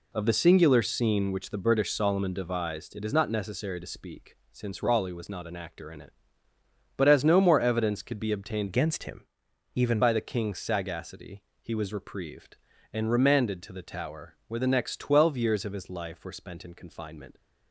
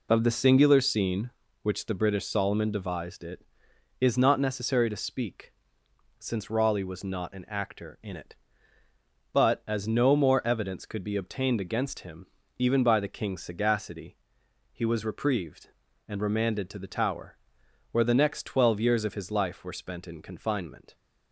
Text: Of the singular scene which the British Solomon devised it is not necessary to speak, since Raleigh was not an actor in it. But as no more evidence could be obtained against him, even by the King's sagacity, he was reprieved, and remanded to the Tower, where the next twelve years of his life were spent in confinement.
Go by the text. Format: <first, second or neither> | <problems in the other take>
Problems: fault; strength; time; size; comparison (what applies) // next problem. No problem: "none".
second | changes voice from "against" to "even"; from 8.6 to 10.0 s; 1.4 s long